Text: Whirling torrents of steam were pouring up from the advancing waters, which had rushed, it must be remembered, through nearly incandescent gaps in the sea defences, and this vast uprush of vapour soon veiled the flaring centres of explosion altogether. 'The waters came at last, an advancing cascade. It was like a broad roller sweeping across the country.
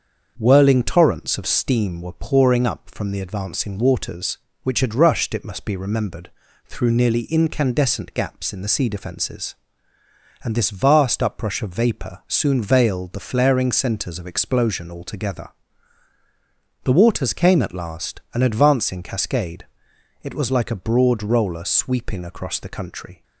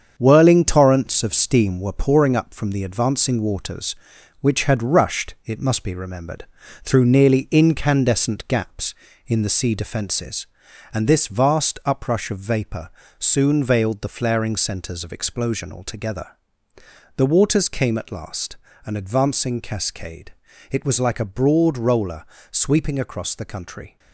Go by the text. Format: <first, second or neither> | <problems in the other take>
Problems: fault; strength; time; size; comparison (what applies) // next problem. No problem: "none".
first | gets quieter; throughout; 6.5 dB // starts louder than the rest; strong; until 1.1 s; 7.5 dB; also in the first // pauses between "vapour" and "soon"; slight; at 12.8 s; 0.30 s long // pauses between "roller" and "sweeping"; slight; at 22.2 s; 0.26 s long